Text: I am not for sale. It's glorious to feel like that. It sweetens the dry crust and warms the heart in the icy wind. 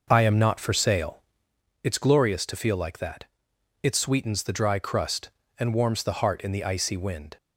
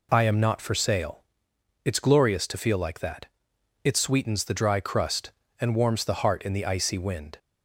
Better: second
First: starts louder than the rest; noticeable; until 1.8 s; 5.5 dB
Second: none

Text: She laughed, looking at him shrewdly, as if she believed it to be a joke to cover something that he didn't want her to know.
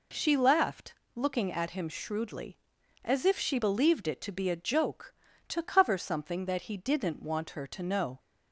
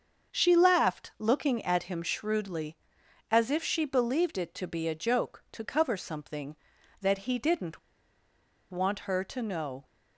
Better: first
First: none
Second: starts louder than the rest; until 1.4 s; 6.5 dB // pauses between "didn't" and "want"; noticeable; at 7.7 s; 0.92 s long

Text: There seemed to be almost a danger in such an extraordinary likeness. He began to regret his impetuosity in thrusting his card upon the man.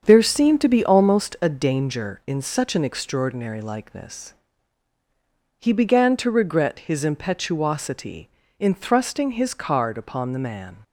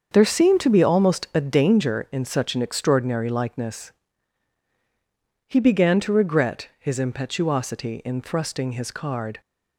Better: first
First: starts louder than the rest; until 1.0 s; 7 dB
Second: starts louder than the rest; until 1.1 s; 7 dB // stops before "upon the man"; at 9.4 s

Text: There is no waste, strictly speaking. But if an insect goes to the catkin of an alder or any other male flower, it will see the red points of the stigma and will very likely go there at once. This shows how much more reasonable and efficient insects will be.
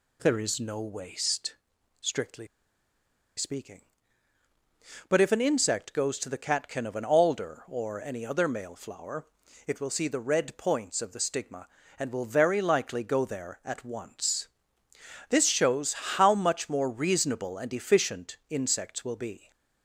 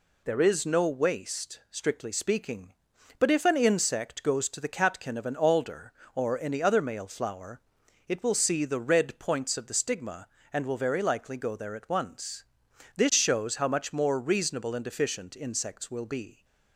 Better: second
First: pauses between "strictly" and "speaking"; noticeable; at 2.4 s; 0.90 s long // pauses between "shows" and "how"; slight; at 15.9 s; 0.20 s long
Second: none

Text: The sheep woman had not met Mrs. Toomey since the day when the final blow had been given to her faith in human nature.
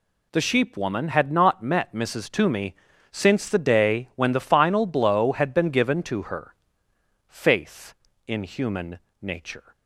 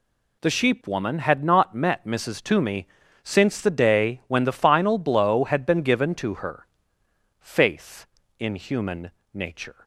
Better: neither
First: pauses between "Toomey" and "since"; at 2.7 s; 0.38 s long // pauses between "her" and "faith"; noticeable; at 6.5 s; 0.74 s long // pauses between "human" and "nature"; slight; at 8.9 s; 0.24 s long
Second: pauses between "Toomey" and "since"; at 2.8 s; 0.38 s long // pauses between "her" and "faith"; noticeable; at 6.6 s; 0.74 s long // pauses between "human" and "nature"; slight; at 9.0 s; 0.24 s long

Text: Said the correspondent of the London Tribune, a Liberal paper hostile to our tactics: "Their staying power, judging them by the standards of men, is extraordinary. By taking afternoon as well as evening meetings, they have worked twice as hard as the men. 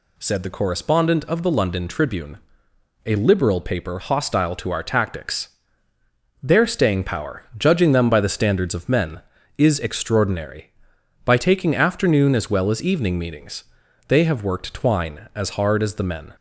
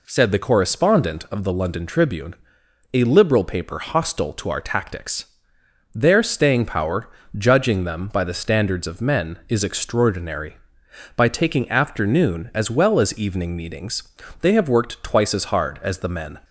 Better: second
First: says "twine" for "twice"; at 14.7 s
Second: none

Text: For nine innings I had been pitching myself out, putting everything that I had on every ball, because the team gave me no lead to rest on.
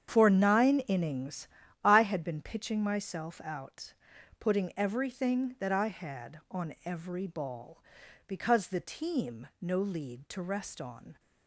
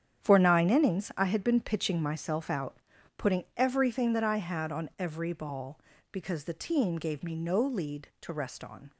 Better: second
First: starts louder than the rest; strong; until 1.1 s; 8 dB // pauses between "innings" and "I"; slight; at 1.4 s; 0.36 s long // skips "gave me"; at 9.5 s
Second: starts louder than the rest; strong; until 1.2 s; 9 dB

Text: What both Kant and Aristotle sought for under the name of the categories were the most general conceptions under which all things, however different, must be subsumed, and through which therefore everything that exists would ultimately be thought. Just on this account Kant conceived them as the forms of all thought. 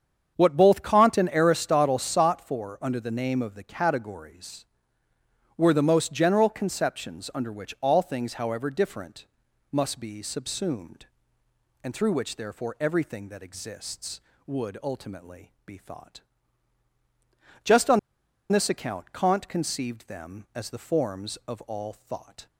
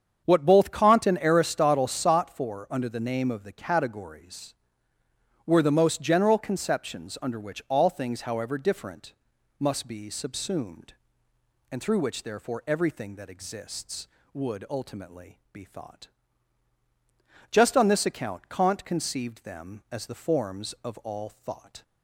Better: second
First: starts louder than the rest; strong; until 1.3 s; 7.5 dB // pauses between "on" and "this"; noticeable; at 17.9 s; 0.52 s long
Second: starts louder than the rest; strong; until 1.2 s; 7.5 dB

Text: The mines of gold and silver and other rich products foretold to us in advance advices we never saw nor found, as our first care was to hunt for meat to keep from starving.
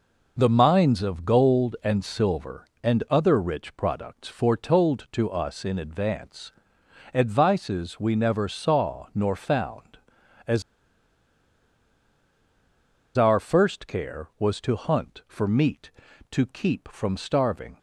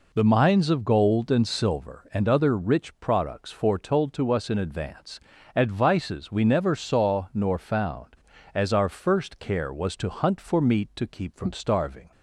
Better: second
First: pauses between "advance" and "advices"; noticeable; at 6.5 s; 0.60 s long // pauses between "as" and "our"; strong; at 10.6 s; 2.5 s long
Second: pauses between "advance" and "advices"; slight; at 5.2 s; 0.36 s long

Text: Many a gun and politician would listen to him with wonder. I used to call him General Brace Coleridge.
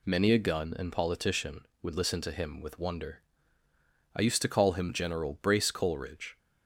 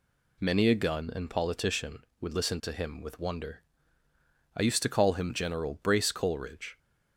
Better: neither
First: none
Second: none

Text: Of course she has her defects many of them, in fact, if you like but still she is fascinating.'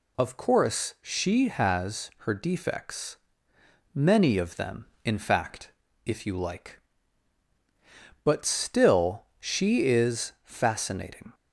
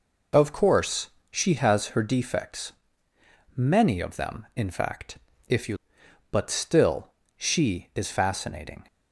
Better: first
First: pauses between "defects" and "many"; noticeable; at 3.1 s; 0.80 s long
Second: pauses between "course" and "she"; slight; at 1.1 s; 0.20 s long // pauses between "defects" and "many"; noticeable; at 2.7 s; 0.84 s long // skips "like"; at 6.0 s // pauses between "still" and "she"; slight; at 7.0 s; 0.30 s long

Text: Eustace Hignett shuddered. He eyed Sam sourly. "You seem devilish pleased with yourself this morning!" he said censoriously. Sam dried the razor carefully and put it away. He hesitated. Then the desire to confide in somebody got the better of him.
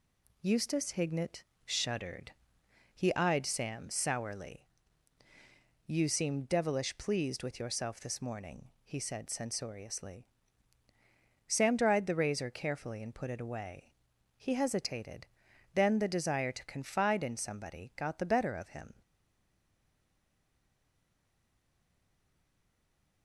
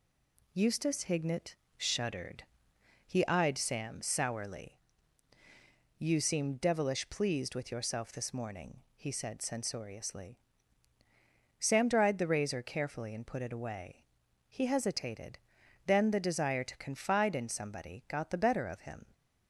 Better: second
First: pauses between "Hignett" and "shuddered"; slight; at 1.4 s; 0.22 s long // stays silent after the last word; strong; from 19.0 s on; 4.2 s long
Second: pauses between "Hignett" and "shuddered"; slight; at 1.5 s; 0.22 s long

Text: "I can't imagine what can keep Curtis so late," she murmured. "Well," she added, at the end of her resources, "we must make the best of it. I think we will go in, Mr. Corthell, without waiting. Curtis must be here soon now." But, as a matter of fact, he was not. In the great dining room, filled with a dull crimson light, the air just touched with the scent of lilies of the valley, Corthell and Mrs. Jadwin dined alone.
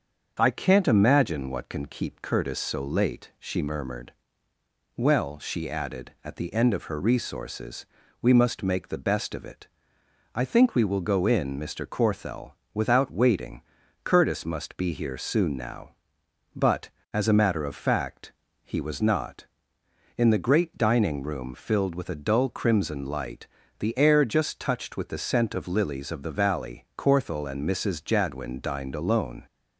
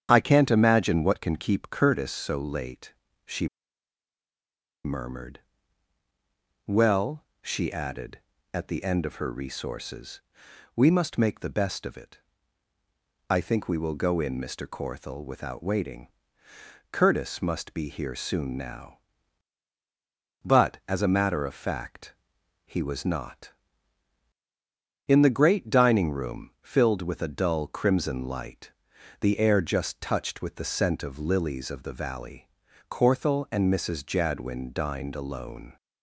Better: first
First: starts louder than the rest; until 1.4 s; 6.5 dB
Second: starts louder than the rest; strong; until 1.1 s; 9 dB // pauses between "she" and "murmured"; strong; at 3.4 s; 1.3 s long

